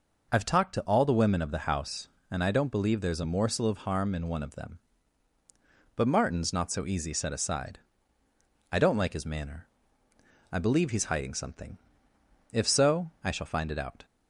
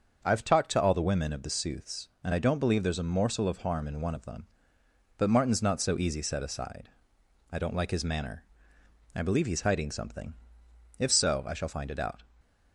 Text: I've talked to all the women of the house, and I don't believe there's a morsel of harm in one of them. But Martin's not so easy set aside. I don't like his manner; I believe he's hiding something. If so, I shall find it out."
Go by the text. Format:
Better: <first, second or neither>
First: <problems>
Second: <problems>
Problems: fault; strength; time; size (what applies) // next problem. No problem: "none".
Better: first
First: none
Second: starts louder than the rest; until 1.2 s; 6.5 dB // says "sooths" for "house"; at 1.4 s